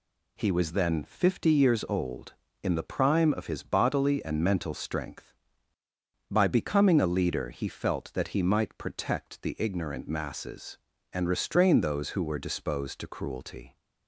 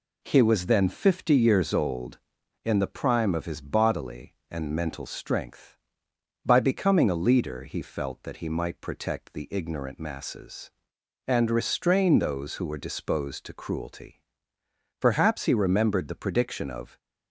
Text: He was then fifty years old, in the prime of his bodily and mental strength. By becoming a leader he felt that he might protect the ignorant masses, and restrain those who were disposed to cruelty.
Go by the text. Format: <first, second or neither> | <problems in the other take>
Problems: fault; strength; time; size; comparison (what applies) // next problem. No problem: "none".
first | goes on to say "Perhaps he remembered the prediction of"; strong; from 14.9 s on; 1.9 s long